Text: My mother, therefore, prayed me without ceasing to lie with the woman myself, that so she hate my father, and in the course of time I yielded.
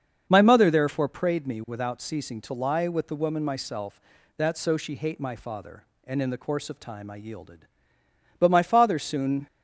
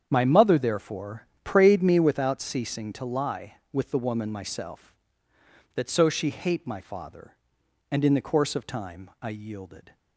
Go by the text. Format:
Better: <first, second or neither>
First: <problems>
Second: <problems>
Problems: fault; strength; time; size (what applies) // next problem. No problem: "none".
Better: second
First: starts louder than the rest; until 1.3 s; 7 dB // goes on to say "But my father soon"; noticeable; from 8.3 s on; 1.0 s long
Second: starts louder than the rest; strong; until 1.1 s; 8 dB